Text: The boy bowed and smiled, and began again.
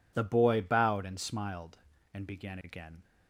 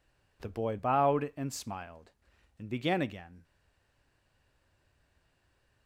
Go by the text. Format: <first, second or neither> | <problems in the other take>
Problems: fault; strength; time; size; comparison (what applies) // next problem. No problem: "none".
first | stays silent after the last word; from 3.4 s on; 2.4 s long